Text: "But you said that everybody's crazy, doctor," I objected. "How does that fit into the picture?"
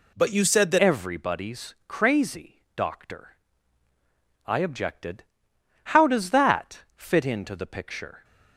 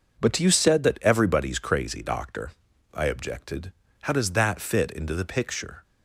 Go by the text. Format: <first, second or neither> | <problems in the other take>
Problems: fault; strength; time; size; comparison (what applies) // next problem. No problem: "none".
second | changes voice at "everybody's"; from 0.7 s on; 7.5 s long